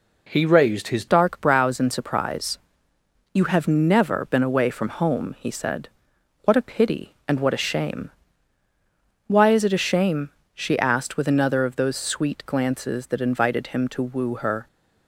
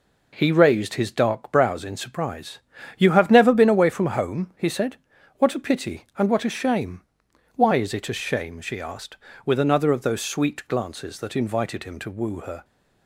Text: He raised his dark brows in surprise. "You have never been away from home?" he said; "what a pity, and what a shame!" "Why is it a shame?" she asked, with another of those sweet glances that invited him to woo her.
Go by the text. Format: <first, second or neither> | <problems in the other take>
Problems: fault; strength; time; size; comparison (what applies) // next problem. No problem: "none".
second | changes voice at "dark"; from 1.0 s on; 13.6 s long